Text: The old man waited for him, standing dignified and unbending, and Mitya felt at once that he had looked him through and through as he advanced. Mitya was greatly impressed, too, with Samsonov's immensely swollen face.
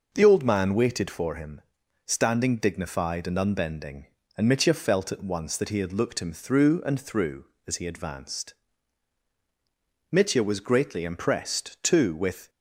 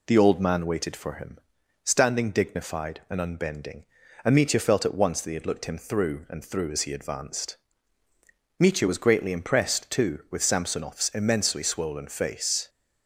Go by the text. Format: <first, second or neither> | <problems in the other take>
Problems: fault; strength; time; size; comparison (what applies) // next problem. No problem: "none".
second | stops before "Samsonov's immensely swollen face"; at 12.4 s